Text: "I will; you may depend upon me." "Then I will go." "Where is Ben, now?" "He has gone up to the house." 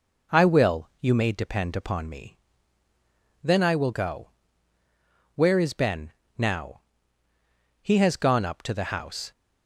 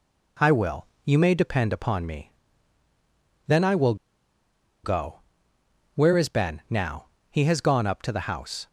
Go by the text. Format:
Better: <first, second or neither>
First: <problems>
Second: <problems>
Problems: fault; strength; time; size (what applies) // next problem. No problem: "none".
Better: first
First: none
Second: pauses between "will" and "go"; noticeable; at 3.9 s; 0.88 s long